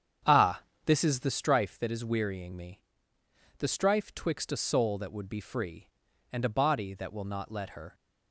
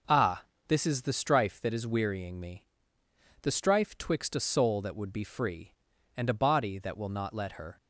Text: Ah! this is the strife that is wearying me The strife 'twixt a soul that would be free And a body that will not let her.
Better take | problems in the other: second | starts louder than the rest; strong; until 1.4 s; 8.5 dB // pauses between "me" and "The"; noticeable; at 2.8 s; 0.78 s long; noticeable in the second

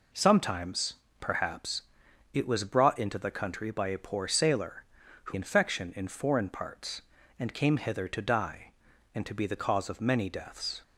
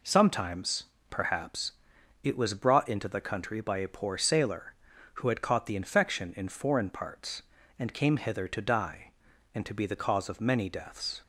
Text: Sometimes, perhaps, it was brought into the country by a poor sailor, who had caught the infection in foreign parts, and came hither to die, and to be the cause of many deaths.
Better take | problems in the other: second | skips "had caught the"; at 5.3 s

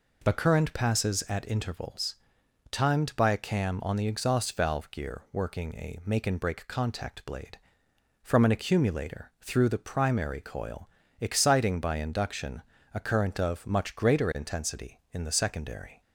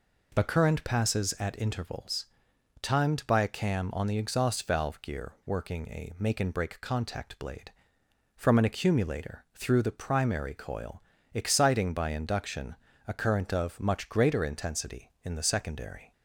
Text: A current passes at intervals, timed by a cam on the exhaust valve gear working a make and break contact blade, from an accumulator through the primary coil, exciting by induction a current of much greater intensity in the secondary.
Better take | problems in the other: neither | pauses between "induction" and "a"; slight; the same in both

